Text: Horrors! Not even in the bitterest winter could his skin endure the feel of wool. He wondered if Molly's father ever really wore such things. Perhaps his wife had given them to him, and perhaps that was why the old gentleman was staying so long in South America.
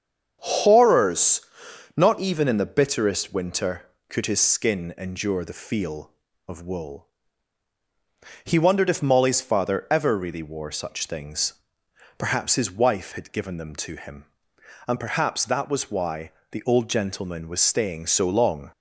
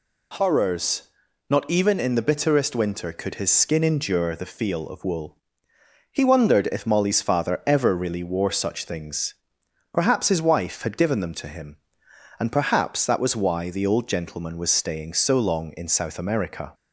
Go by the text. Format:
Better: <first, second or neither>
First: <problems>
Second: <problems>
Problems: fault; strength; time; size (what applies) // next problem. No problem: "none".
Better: second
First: starts louder than the rest; strong; until 1.4 s; 7 dB // pauses between "why" and "the"; slight; at 16.3 s; 0.20 s long // stops before "in South America"; at 18.7 s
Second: none